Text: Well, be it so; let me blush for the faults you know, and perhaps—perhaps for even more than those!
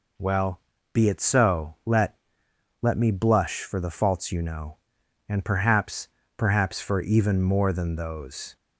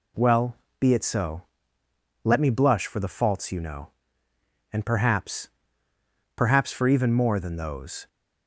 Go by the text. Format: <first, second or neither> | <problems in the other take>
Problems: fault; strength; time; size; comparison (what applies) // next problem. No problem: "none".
second | says "let" twice; at 2.8 s